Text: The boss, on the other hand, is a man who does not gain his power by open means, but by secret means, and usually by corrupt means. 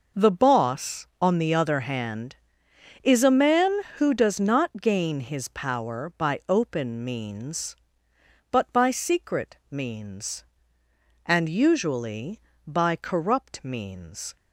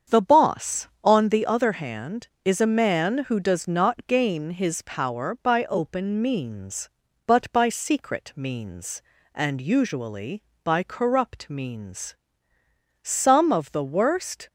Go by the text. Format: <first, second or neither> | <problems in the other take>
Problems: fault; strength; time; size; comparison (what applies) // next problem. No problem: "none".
first | starts louder than the rest; strong; until 1.2 s; 7.5 dB // goes on to say "Some of the worst"; from 13.0 s on; 1.4 s long